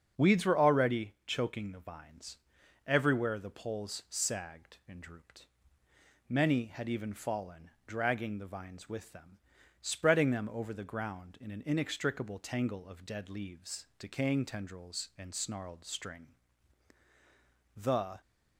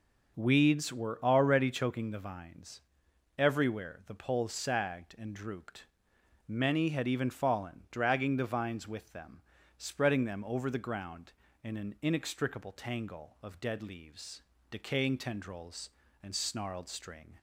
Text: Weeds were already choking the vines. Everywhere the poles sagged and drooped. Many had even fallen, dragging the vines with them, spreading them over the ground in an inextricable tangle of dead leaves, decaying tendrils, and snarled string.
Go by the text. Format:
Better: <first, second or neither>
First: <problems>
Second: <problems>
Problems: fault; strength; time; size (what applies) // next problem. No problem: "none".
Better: second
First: starts louder than the rest; until 1.3 s; 7 dB // goes on to say "The"; slight; from 17.7 s on; 0.44 s long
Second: none